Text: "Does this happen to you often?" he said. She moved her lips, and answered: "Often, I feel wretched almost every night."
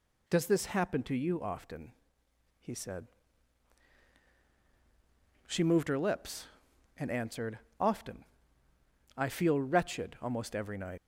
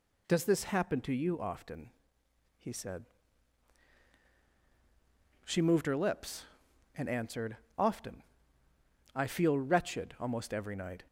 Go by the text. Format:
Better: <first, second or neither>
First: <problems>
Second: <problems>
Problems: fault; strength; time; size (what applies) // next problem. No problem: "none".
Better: second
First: leaves "night" unfinished; at 10.9 s; 105 ms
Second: none